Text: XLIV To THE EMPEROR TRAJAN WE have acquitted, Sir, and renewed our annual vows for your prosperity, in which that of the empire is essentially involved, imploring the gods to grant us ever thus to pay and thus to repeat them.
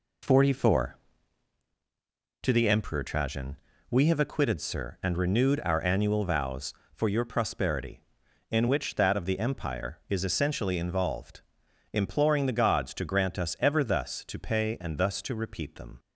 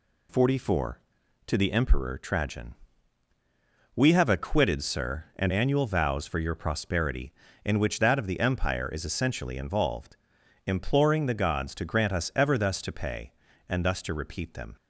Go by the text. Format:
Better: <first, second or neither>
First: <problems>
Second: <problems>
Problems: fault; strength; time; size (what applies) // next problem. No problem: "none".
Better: first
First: pauses between "TRAJAN" and "WE"; slight; at 3.5 s; 0.32 s long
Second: pauses between "TRAJAN" and "WE"; at 2.7 s; 1.2 s long // skips "renewed our"; at 5.5 s